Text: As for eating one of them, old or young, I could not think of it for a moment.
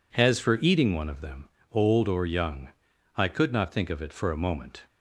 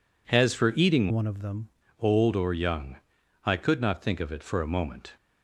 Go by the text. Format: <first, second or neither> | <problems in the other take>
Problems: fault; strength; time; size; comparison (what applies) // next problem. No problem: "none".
first | changes voice from "one" to "them"; from 1.1 to 1.6 s; 0.5 s long